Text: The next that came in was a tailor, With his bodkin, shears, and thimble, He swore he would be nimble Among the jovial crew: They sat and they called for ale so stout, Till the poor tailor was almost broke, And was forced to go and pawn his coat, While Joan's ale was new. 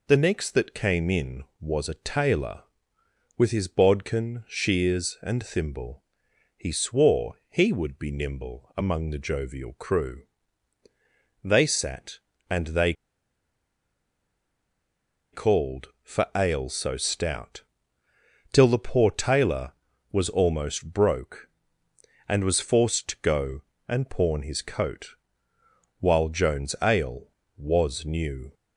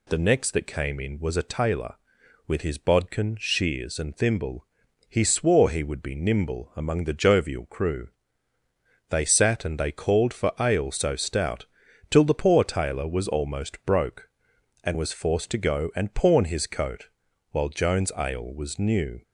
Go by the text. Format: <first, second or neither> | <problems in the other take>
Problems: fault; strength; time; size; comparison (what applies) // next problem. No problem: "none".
second | pauses between "they" and "called"; strong; at 12.9 s; 2.4 s long